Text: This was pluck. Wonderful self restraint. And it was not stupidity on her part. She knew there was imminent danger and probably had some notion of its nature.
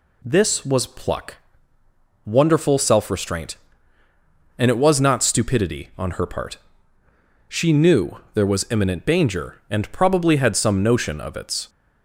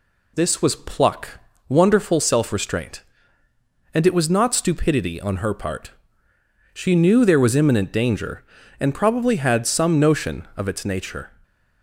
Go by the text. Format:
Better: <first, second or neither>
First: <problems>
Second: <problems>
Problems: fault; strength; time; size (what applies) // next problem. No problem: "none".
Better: second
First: stops before "nature"; at 11.6 s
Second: none